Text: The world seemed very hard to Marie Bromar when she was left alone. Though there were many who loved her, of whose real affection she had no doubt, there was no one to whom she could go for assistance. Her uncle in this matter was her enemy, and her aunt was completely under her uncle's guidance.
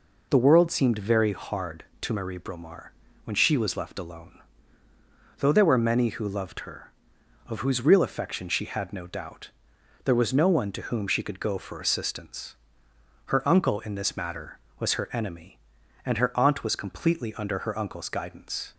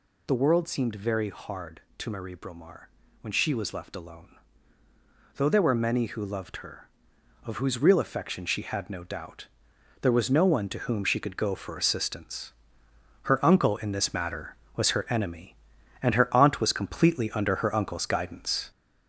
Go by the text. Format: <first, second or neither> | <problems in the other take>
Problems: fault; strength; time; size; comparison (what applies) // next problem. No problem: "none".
first | gets louder; noticeable; throughout; 4.5 dB // pauses between "Bromar" and "when"; slight; at 2.8 s; 0.36 s long; slight in the first